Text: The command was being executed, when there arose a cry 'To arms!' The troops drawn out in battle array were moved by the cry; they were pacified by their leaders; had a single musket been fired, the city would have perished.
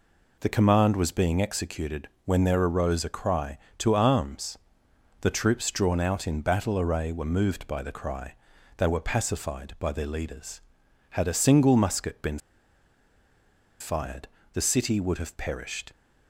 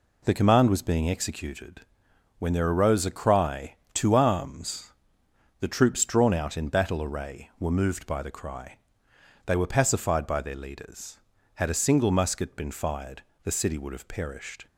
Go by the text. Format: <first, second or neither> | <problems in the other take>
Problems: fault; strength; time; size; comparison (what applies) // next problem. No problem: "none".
second | pauses between "been" and "fired"; strong; at 12.3 s; 1.4 s long